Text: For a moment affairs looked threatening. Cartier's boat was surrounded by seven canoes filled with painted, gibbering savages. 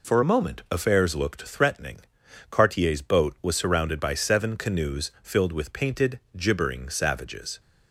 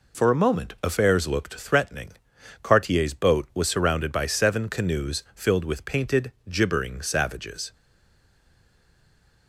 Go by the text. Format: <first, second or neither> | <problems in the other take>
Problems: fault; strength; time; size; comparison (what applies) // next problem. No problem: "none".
first | stays silent after the last word; noticeable; from 7.7 s on; 1.7 s long